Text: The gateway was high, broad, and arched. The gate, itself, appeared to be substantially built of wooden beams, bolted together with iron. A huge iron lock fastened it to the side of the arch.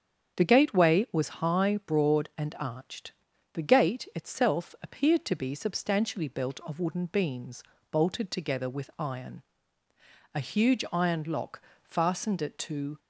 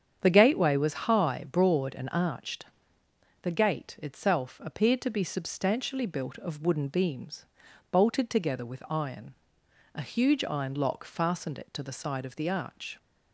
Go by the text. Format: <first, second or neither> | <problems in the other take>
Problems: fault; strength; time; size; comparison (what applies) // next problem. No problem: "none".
second | starts louder than the rest; strong; until 1.4 s; 7.5 dB; strong in the second // pauses between "lock" and "fastened"; slight; at 11.6 s; 0.26 s long // stops before "the side of the arch"; at 12.9 s